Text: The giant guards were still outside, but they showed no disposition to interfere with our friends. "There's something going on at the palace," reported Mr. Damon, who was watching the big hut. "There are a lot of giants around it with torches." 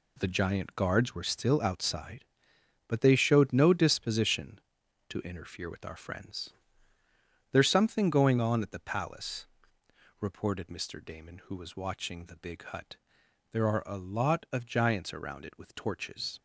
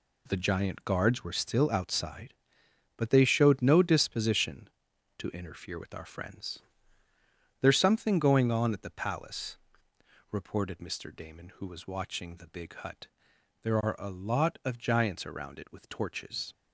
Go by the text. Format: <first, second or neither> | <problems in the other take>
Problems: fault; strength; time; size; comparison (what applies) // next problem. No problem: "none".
neither | none